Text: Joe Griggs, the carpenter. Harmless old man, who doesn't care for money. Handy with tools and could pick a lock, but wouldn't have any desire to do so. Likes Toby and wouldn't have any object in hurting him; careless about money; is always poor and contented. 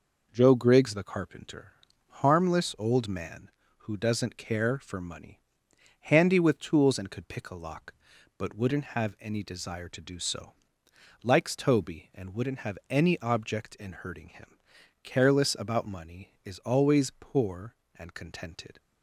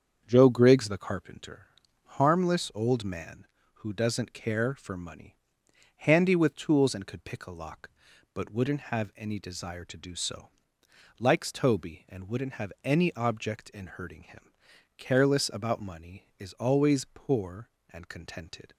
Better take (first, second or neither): first